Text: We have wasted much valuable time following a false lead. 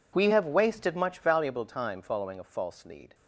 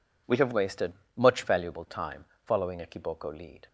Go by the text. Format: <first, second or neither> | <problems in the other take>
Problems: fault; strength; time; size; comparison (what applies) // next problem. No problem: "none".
first | pauses between "wasted" and "much"; slight; at 0.9 s; 0.24 s long // pauses between "time" and "following"; slight; at 2.2 s; 0.22 s long // says "kiboko" for "false"; at 2.8 s